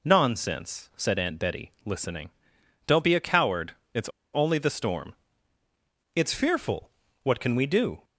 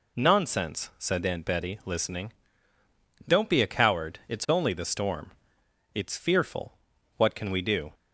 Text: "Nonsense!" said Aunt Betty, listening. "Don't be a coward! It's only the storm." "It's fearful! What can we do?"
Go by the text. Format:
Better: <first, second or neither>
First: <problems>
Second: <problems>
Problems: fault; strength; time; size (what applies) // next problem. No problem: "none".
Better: second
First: pauses between "It's" and "only"; slight; at 4.0 s; 0.24 s long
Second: none